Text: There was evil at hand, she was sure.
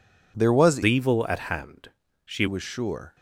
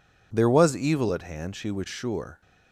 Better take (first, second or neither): second